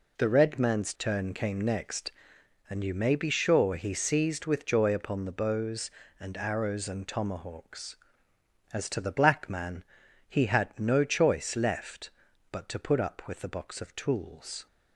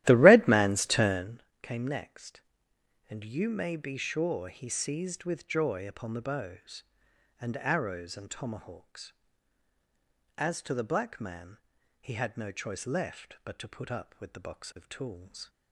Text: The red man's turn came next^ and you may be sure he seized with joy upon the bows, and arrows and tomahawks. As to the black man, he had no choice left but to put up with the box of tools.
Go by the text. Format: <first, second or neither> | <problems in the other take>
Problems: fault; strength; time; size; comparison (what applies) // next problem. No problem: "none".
first | starts louder than the rest; strong; until 1.4 s; 14.5 dB // pauses between "turn" and "came"; slight; at 1.4 s; 0.20 s long